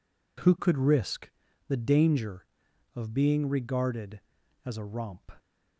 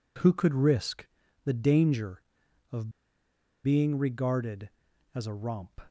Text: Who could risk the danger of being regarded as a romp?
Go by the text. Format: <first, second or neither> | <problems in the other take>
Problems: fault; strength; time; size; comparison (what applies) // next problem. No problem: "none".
first | pauses between "risk" and "the"; at 1.0 s; 0.40 s long; also in the first // pauses between "of" and "being"; noticeable; at 2.8 s; 0.75 s long